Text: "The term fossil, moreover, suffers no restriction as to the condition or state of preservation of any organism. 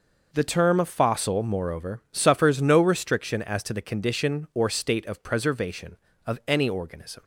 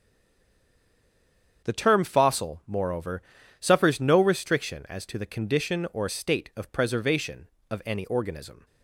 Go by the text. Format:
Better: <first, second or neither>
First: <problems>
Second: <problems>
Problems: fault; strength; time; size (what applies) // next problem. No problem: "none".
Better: first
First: none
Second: stays silent before the first word; noticeable; until 1.6 s; 1.6 s long // starts louder than the rest; strong; until 2.7 s; 7.5 dB